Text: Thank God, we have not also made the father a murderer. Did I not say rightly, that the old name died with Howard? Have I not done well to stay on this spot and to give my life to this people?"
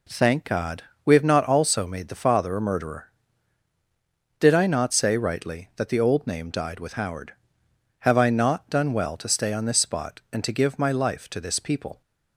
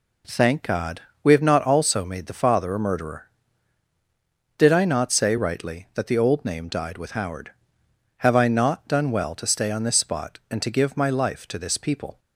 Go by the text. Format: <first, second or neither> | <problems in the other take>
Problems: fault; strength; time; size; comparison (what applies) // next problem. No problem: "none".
neither | none